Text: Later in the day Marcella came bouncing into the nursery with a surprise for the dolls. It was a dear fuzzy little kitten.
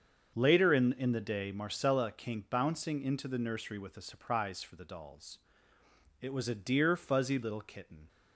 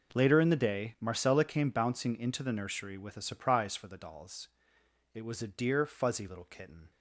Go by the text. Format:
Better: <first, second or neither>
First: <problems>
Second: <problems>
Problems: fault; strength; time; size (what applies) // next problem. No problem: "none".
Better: second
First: starts louder than the rest; until 1.3 s; 7 dB // says "in" twice; at 0.9 s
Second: none